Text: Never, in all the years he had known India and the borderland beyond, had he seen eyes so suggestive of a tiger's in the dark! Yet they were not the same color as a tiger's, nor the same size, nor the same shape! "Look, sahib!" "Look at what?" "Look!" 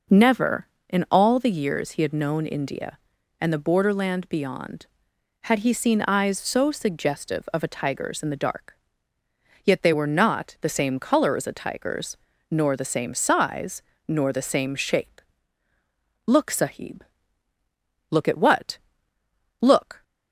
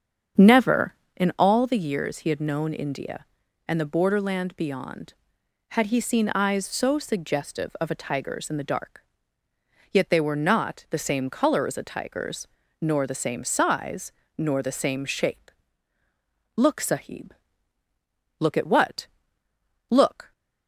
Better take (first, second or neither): first